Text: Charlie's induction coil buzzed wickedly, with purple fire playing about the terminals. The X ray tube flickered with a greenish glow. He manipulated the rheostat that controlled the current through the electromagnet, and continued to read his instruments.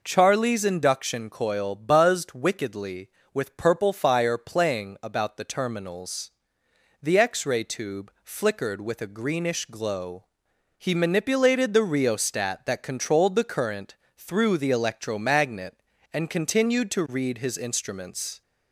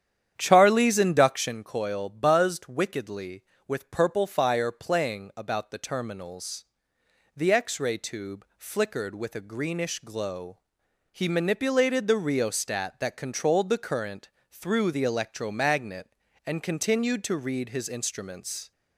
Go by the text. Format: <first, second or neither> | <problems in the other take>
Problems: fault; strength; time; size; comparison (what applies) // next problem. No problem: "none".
first | starts louder than the rest; strong; until 1.6 s; 9.5 dB // pauses between "current" and "through"; slight; at 14.2 s; 0.24 s long; slight in the first